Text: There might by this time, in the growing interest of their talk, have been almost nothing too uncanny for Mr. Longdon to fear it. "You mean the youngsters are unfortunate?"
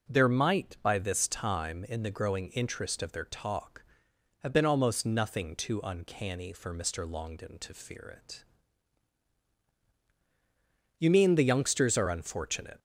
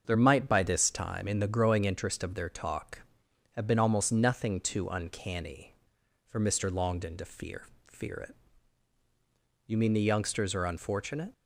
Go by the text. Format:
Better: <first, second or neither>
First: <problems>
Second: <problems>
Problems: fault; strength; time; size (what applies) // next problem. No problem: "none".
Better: first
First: starts louder than the rest; noticeable; until 1.1 s; 6 dB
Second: starts louder than the rest; until 1.0 s; 7 dB // says "fear" twice; at 7.8 s